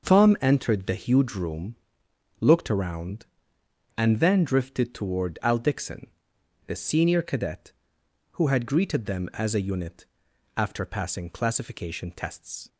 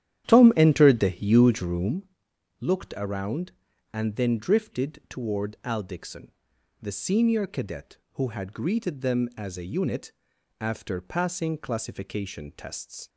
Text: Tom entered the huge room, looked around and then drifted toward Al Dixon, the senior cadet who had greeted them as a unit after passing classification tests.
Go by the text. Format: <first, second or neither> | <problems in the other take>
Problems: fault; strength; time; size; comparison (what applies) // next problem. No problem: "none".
first | starts louder than the rest; strong; until 2.0 s; 11 dB // pauses between "unit" and "after"; noticeable; at 10.1 s; 0.48 s long; noticeable in the first